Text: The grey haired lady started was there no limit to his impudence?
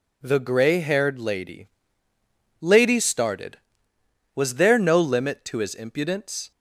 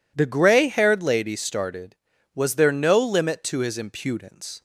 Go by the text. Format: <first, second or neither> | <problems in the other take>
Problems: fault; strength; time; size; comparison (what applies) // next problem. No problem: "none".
second | says "lady" twice; at 2.6 s